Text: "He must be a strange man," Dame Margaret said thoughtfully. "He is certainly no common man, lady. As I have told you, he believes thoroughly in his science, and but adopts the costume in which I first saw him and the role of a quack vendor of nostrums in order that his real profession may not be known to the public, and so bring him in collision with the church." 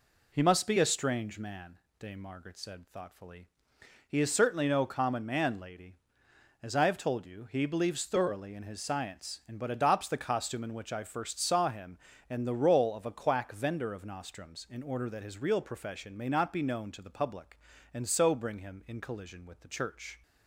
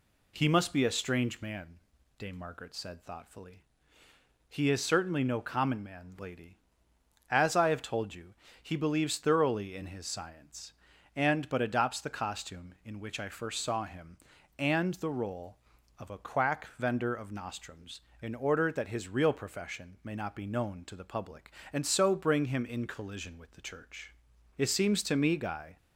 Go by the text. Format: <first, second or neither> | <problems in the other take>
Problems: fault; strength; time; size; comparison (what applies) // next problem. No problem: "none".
first | goes on to say "It seems to me Guy"; noticeable; from 24.5 s on; 1.2 s long